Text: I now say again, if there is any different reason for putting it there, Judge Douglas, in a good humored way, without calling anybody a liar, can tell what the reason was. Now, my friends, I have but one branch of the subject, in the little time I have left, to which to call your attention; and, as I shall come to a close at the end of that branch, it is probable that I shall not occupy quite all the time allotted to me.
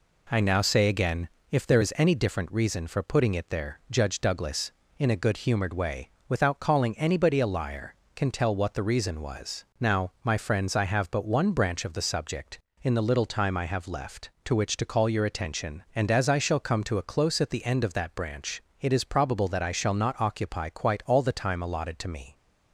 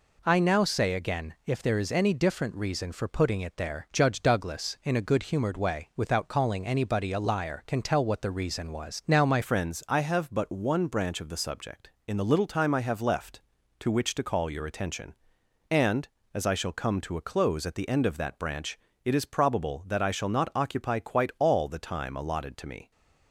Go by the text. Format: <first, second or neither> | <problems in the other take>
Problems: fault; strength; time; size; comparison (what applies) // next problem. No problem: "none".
first | changes voice at "friends"; from 9.4 s on; 13.5 s long